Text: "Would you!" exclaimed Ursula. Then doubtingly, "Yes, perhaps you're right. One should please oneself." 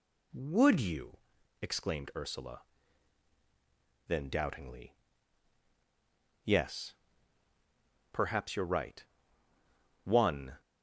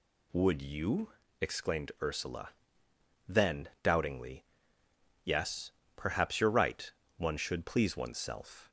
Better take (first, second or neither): second